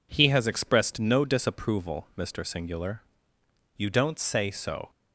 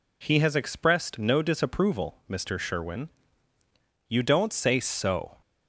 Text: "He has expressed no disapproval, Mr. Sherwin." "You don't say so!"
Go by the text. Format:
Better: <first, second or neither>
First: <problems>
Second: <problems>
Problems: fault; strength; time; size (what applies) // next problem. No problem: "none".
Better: second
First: says "Singular" for "Sherwin"; at 2.4 s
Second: none